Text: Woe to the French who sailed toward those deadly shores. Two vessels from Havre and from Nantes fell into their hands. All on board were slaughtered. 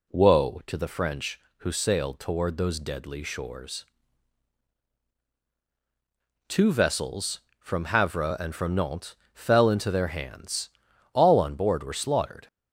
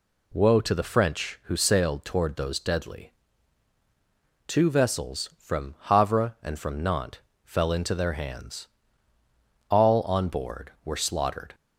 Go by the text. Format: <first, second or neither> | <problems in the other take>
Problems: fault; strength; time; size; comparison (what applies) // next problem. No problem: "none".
first | skips "shores"; at 3.7 s // pauses between "Nantes" and "fell"; slight; at 7.1 s; 0.26 s long; slight in the first